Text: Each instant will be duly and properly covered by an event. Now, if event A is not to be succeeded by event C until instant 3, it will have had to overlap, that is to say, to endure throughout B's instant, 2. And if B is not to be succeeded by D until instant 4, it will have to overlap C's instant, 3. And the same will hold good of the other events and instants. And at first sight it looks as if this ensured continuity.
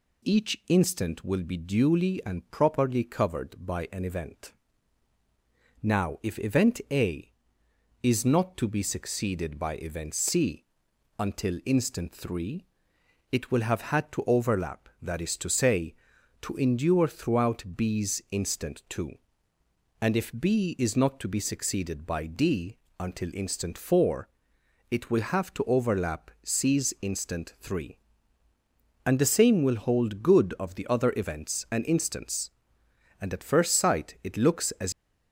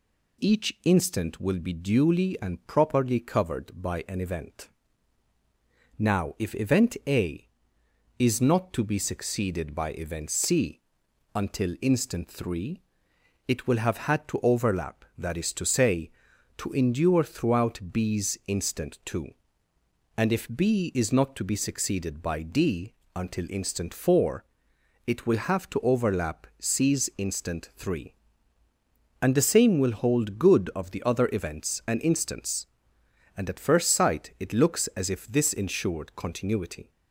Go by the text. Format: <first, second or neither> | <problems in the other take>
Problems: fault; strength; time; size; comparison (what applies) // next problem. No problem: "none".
second | pauses between "C" and "until"; noticeable; at 10.6 s; 0.56 s long; noticeable in the second // pauses between "D" and "until"; slight; at 22.7 s; 0.22 s long; slight in the second // stops before "if this ensured continuity"; at 34.9 s